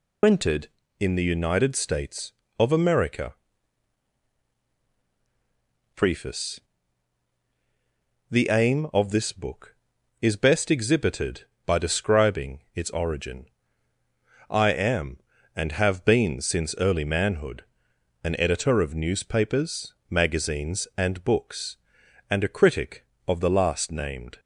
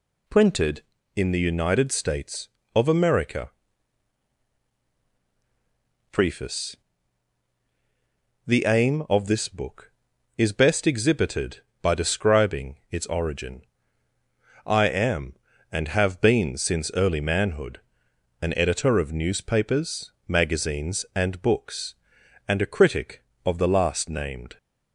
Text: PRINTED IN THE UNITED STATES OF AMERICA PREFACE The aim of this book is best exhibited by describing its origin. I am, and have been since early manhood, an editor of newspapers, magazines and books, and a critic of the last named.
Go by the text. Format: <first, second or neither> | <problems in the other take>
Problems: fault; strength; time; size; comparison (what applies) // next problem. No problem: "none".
second | loses the start of "PRINTED"; at 0.2 s; 80 ms // pauses between "AMERICA" and "PREFACE"; strong; at 3.3 s; 2.6 s long; strong in the second // pauses between "PREFACE" and "The"; strong; at 6.5 s; 1.7 s long; strong in the second